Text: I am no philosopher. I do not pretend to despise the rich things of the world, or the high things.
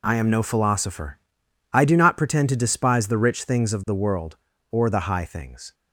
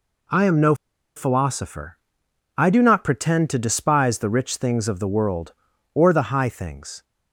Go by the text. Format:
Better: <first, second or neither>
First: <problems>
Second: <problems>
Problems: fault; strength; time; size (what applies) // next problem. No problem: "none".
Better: first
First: none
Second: pauses between "no" and "philosopher"; at 0.7 s; 0.42 s long